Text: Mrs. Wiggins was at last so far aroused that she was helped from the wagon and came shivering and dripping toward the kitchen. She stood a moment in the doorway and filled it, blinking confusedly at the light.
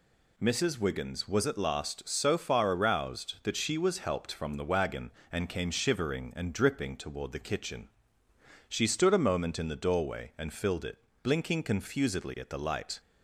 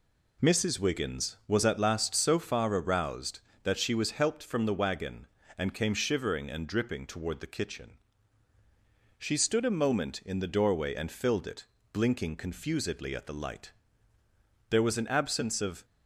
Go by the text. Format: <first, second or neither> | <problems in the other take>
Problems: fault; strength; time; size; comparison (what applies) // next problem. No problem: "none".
first | goes on to say "There was an absence of"; noticeable; from 14.6 s on; 1.1 s long